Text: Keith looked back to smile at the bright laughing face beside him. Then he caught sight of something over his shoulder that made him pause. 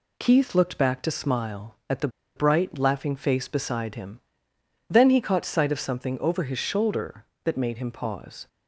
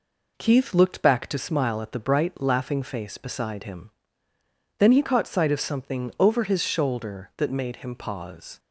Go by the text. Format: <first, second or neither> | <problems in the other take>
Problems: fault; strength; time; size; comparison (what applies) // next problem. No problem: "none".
second | pauses between "the" and "bright"; slight; at 2.0 s; 0.27 s long